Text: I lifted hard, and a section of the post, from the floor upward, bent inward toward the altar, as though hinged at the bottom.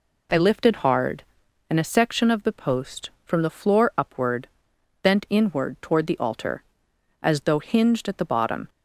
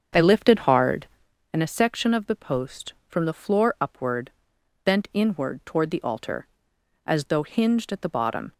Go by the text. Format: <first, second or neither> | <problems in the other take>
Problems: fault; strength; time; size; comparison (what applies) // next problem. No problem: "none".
first | starts louder than the rest; until 1.3 s; 7 dB